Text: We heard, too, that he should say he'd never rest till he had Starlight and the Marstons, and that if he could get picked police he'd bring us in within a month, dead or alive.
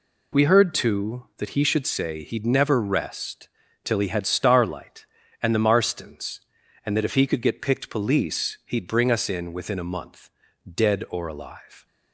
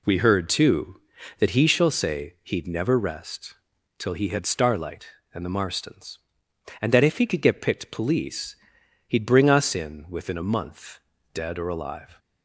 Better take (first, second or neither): first